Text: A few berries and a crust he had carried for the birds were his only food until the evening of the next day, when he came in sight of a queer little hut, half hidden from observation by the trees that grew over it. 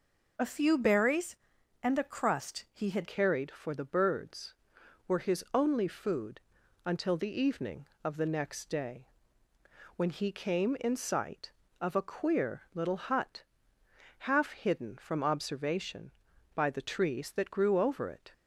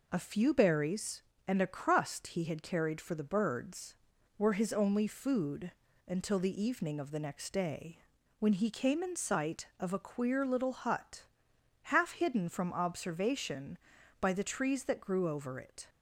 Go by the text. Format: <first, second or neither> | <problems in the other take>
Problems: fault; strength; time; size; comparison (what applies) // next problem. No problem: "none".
second | changes voice at "carried"; from 3.0 s on; 15.3 s long // pauses between "food" and "until"; noticeable; at 6.3 s; 0.46 s long; slight in the second